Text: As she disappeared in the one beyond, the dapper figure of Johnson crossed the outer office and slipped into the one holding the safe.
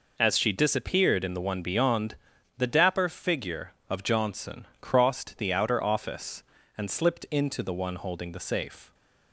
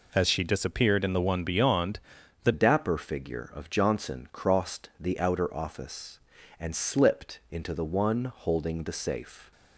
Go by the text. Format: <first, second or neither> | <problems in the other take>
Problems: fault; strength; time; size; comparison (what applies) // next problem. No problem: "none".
first | changes voice at "dapper"; from 2.5 s on; 7.0 s long